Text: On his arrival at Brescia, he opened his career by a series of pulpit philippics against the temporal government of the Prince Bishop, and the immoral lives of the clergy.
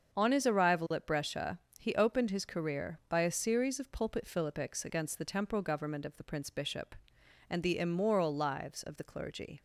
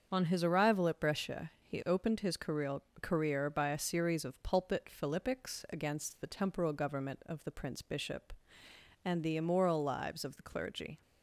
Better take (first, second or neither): first